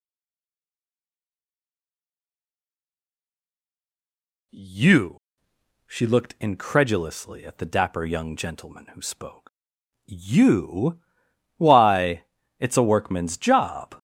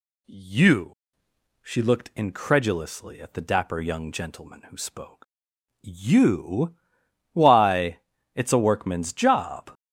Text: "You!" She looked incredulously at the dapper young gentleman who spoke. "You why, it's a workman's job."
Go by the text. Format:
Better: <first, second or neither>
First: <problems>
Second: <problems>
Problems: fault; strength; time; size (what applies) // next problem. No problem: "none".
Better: second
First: stays silent before the first word; strong; until 4.5 s; 4.5 s long // pauses between "You" and "why"; noticeable; at 11.0 s; 0.56 s long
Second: pauses between "You" and "why"; noticeable; at 6.7 s; 0.56 s long